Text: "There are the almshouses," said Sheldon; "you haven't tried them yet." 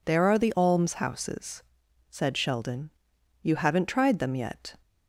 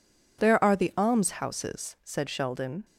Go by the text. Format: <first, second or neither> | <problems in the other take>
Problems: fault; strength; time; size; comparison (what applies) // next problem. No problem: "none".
first | stops before "you haven't tried them yet"; at 2.8 s